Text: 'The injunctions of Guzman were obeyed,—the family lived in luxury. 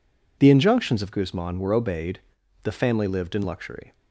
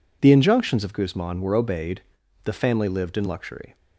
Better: neither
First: none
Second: none

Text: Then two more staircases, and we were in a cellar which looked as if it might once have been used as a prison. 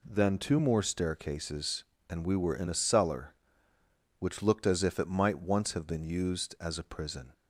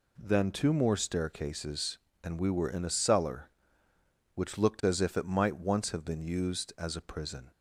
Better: neither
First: none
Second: none

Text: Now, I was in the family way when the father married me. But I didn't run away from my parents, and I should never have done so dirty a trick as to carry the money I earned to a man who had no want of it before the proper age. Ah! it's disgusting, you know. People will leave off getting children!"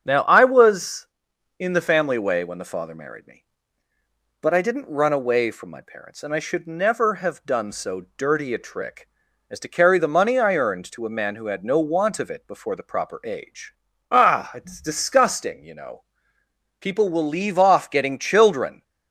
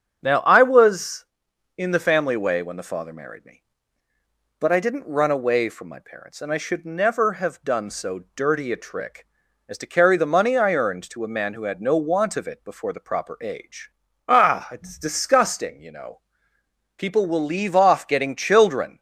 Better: neither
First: starts louder than the rest; strong; until 1.0 s; 8 dB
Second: starts louder than the rest; strong; until 1.2 s; 8 dB

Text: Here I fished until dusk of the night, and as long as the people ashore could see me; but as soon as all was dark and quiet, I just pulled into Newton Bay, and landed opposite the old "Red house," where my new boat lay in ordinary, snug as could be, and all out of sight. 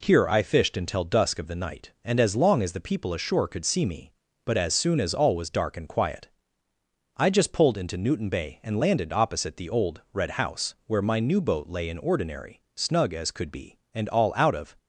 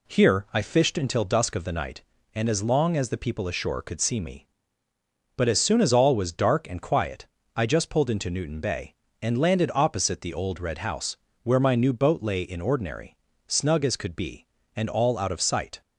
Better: second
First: stops before "sight"; at 14.7 s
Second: none

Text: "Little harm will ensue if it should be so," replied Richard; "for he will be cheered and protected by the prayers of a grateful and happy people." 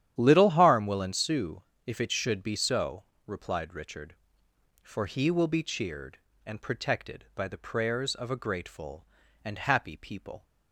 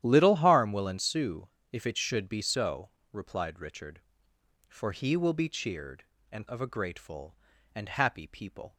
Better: first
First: starts louder than the rest; strong; until 1.1 s; 10.5 dB // pauses between "ensue" and "if"; slight; at 1.6 s; 0.24 s long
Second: starts louder than the rest; strong; until 1.0 s; 11.5 dB // pauses between "ensue" and "if"; slight; at 1.4 s; 0.24 s long // skips "protected by the prayers"; at 6.4 s

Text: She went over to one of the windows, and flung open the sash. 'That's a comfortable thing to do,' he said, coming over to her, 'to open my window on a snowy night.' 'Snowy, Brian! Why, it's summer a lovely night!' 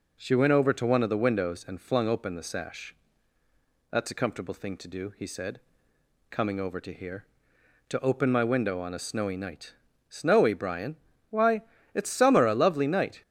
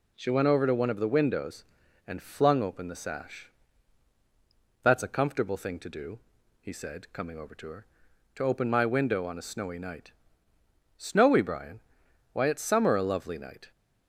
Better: second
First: says "here" for "her"; at 6.9 s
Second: none

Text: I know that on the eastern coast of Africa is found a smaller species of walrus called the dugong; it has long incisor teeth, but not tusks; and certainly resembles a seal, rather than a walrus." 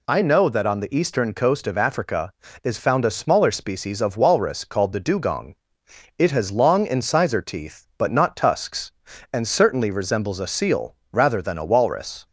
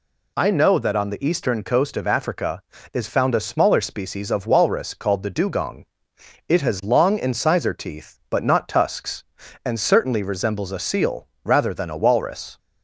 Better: neither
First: none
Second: none

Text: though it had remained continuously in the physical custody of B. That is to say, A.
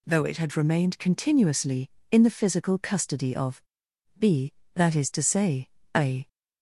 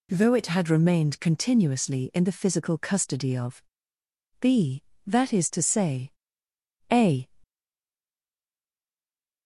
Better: first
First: pauses between "of" and "B"; noticeable; at 3.6 s; 0.56 s long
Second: pauses between "of" and "B"; noticeable; at 3.6 s; 0.78 s long // stays silent after the last word; noticeable; from 7.4 s on; 2.0 s long

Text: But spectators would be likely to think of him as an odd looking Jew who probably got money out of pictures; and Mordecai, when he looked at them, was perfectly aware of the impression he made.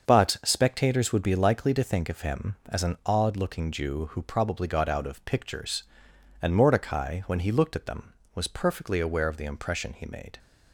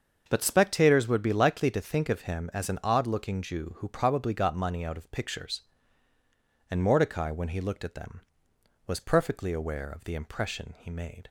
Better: second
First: starts louder than the rest; until 1.1 s; 6.5 dB // skips "money"; at 4.8 s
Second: starts louder than the rest; until 1.3 s; 6.5 dB

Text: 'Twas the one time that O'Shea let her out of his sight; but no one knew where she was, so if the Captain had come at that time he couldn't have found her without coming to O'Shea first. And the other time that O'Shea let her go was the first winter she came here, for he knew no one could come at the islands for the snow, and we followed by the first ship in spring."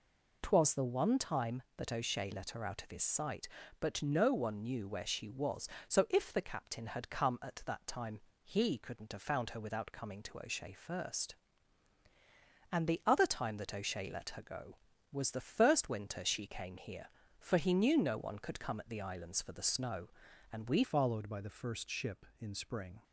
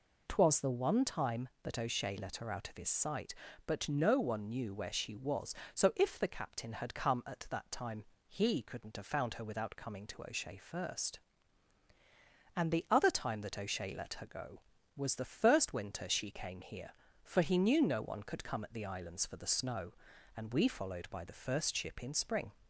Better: second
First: pauses between "time" and "he"; slight; at 8.1 s; 0.22 s long // changes voice at "followed"; from 20.8 s on; 2.2 s long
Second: pauses between "time" and "he"; slight; at 8.0 s; 0.22 s long

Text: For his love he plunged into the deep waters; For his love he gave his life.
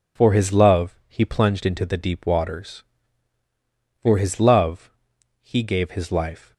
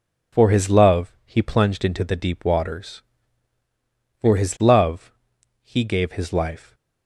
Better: neither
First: pauses between "love" and "he"; noticeable; at 4.8 s; 0.52 s long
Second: pauses between "love" and "he"; noticeable; at 5.0 s; 0.52 s long

